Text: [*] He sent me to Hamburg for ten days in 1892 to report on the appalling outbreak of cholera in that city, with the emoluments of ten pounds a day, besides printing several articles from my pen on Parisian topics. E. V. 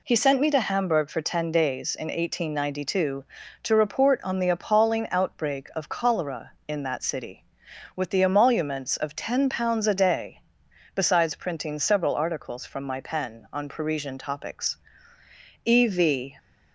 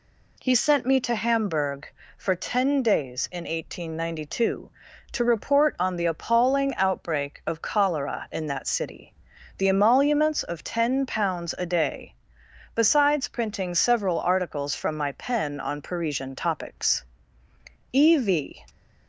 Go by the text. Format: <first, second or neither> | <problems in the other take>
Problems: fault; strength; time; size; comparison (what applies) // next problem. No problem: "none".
first | skips "with"; at 9.3 s